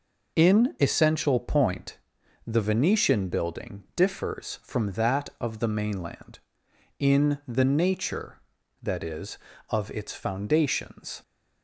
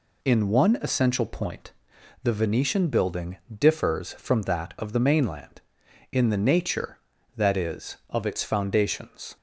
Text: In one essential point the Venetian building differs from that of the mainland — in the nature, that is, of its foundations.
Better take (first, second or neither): second